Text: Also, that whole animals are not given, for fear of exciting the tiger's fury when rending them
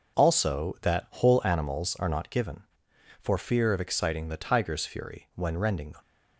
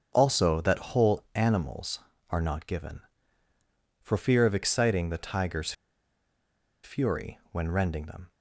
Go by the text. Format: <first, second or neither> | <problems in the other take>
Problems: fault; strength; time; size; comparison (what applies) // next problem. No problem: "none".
first | starts louder than the rest; until 1.1 s; 7 dB // pauses between "tiger's" and "fury"; at 5.7 s; 1.1 s long